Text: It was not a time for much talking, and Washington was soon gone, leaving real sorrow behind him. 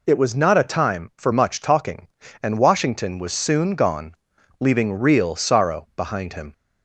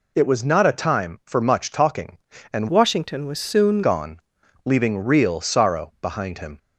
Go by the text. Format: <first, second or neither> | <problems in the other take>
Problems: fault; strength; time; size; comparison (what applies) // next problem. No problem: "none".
first | changes voice from "Washington" to "soon"; from 2.6 to 3.8 s; 1.2 s long